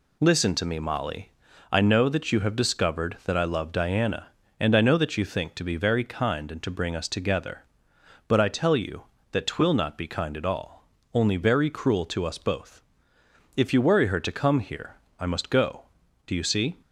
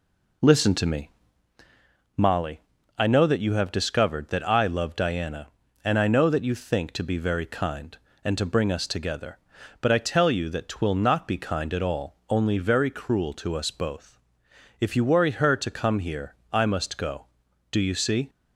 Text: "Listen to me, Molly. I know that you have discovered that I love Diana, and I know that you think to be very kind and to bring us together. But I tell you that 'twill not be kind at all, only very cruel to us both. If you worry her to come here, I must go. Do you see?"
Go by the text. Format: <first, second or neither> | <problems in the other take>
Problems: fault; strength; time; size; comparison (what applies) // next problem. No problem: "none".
first | starts louder than the rest; until 1.6 s; 3.5 dB